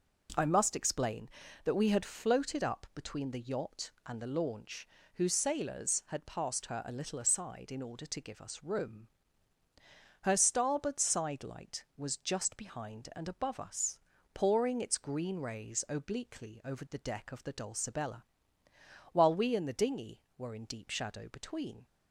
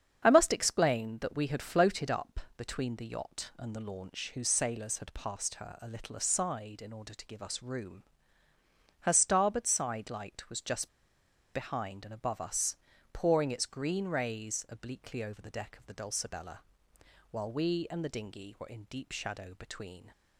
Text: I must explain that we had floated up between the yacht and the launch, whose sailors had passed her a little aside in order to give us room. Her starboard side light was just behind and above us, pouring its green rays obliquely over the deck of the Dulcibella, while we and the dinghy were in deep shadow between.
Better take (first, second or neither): first